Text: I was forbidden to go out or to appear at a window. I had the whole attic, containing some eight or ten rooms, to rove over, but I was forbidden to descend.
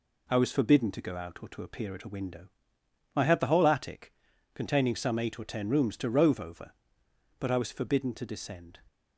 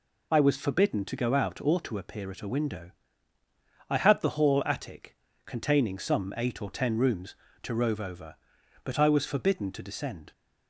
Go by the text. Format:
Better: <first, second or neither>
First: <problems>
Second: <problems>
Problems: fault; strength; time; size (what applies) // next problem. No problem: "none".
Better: first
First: none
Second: says "hall" for "whole"; at 4.2 s